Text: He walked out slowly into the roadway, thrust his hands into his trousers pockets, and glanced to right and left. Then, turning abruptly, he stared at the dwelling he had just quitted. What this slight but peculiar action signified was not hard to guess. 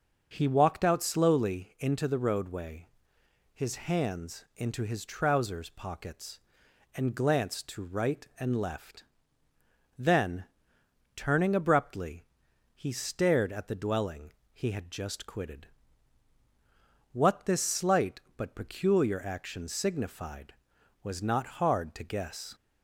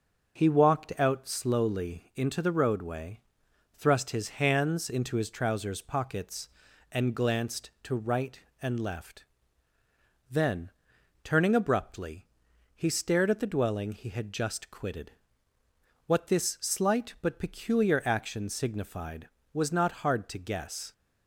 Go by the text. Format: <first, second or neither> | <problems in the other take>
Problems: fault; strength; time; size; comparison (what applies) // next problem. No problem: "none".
second | starts louder than the rest; until 1.3 s; 6 dB; noticeable in the second // skips "thrust"; at 3.1 s // pauses between "dwelling" and "he"; slight; at 14.3 s; 0.22 s long